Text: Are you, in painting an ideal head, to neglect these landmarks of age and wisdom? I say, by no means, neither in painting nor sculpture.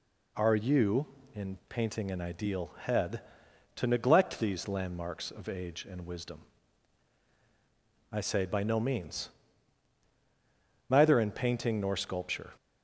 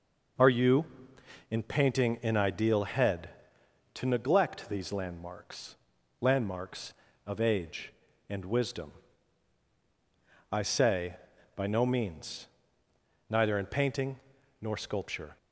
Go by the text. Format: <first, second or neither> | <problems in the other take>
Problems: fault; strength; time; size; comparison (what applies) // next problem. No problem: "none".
first | says "landmarks" twice; at 6.2 s // pauses between "painting" and "nor"; at 14.1 s; 0.42 s long